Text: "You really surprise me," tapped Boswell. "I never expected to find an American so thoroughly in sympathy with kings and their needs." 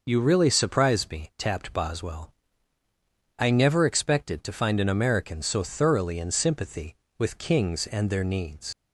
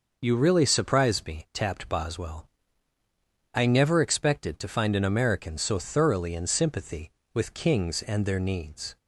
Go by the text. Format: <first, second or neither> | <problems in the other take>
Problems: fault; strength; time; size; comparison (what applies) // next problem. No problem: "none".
second | leaves "needs" unfinished; at 8.7 s; 85 ms